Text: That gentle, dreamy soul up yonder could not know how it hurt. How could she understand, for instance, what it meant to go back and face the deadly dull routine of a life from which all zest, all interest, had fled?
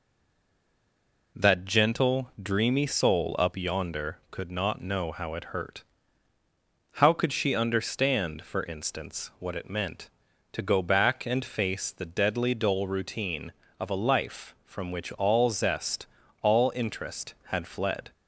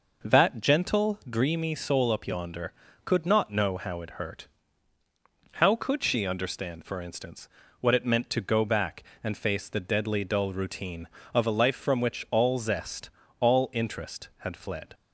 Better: second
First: stays silent before the first word; noticeable; until 1.3 s; 1.3 s long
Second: none

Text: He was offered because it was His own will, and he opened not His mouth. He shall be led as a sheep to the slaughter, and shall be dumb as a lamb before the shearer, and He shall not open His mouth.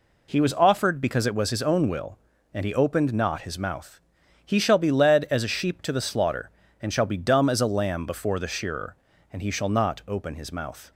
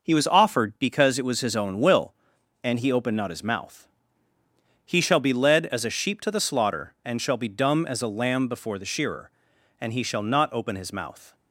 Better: neither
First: none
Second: none

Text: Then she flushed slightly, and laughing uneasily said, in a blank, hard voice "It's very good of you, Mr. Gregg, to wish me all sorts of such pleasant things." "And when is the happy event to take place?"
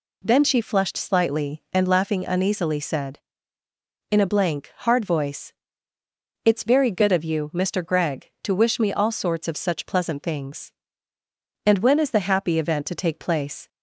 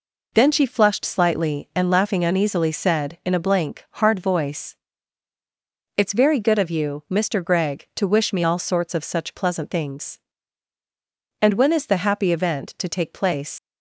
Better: first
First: pauses between "voice" and "It's"; noticeable; at 5.5 s; 0.92 s long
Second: pauses between "voice" and "It's"; at 4.7 s; 1.2 s long // leaves "place" unfinished; at 13.5 s; 70 ms

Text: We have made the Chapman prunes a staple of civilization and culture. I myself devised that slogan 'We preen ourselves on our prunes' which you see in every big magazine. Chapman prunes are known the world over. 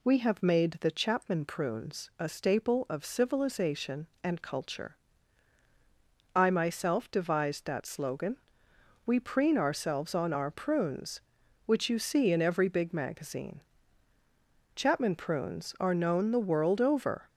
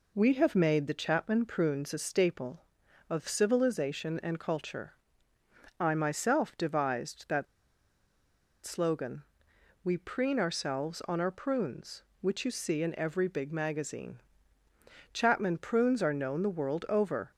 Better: first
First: pauses between "slogan" and "We"; noticeable; at 8.3 s; 0.70 s long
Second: pauses between "that" and "slogan"; at 7.4 s; 1.1 s long // pauses between "slogan" and "We"; noticeable; at 9.2 s; 0.62 s long

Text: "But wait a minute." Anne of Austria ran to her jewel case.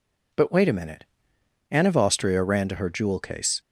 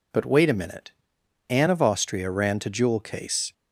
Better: first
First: none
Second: skips "her"; at 2.7 s

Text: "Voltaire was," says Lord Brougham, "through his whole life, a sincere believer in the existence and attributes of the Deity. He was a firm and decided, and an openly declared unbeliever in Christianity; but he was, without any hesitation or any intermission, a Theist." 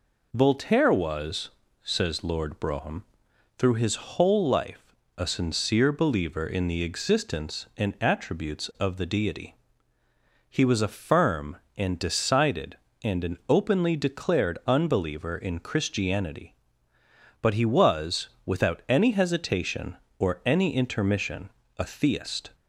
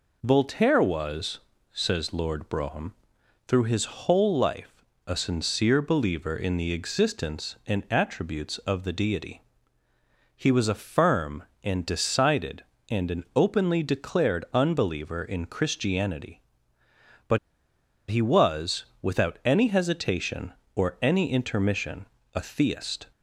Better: first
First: none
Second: pauses between "but" and "he"; noticeable; at 17.3 s; 0.71 s long

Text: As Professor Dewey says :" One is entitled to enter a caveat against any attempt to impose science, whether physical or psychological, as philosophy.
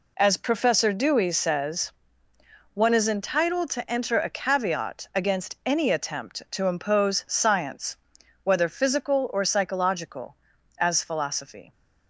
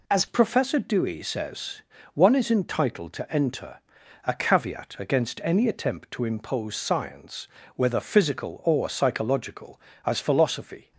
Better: first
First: none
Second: changes voice at "Professor"; from 0.2 s on; 10.7 s long // pauses between "enter" and "a"; at 3.7 s; 0.44 s long

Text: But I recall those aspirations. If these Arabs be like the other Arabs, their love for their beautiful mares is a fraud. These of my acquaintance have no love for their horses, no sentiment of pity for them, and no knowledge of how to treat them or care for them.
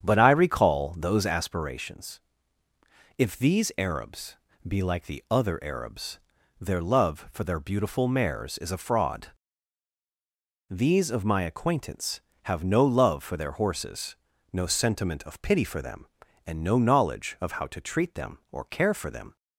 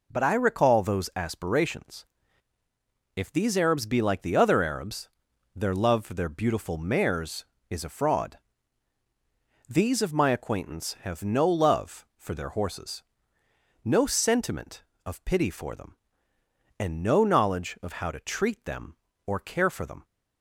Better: second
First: starts louder than the rest; strong; until 1.6 s; 8 dB // pauses between "Arabs" and "be"; slight; at 4.3 s; 0.32 s long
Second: none

